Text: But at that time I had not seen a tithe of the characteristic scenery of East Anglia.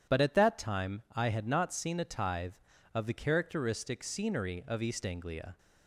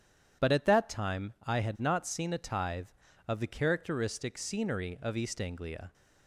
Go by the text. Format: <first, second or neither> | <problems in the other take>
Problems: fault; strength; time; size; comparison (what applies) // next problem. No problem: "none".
neither | none